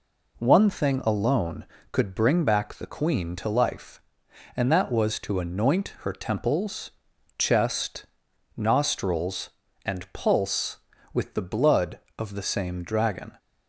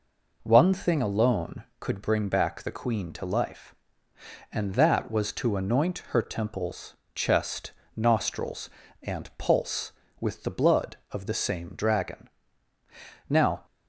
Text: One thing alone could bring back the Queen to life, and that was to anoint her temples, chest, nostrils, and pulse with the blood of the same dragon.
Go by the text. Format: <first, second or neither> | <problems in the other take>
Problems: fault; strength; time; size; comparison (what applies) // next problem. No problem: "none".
first | goes on to say "Now"; slight; from 13.2 s on; 0.36 s long